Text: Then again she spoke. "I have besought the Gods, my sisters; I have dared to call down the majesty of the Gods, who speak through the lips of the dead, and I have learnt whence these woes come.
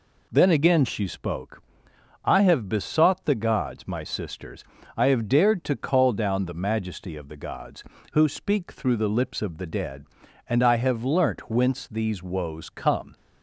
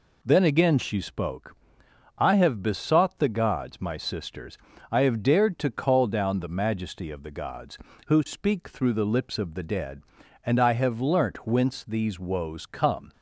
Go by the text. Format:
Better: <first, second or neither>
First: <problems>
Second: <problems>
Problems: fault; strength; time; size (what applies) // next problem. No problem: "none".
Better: neither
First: none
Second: none